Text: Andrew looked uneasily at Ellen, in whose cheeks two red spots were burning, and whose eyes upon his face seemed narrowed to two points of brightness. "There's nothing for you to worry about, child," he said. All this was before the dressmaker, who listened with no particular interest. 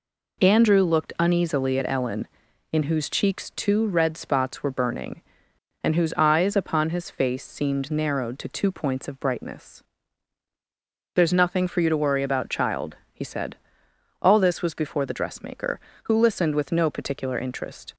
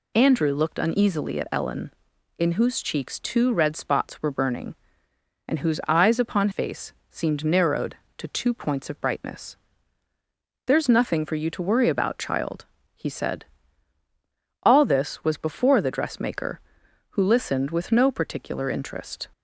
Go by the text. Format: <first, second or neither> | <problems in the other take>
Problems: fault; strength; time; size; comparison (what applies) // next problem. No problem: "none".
first | skips "his"; at 6.5 s // pauses between "face" and "seemed"; slight; at 6.9 s; 0.18 s long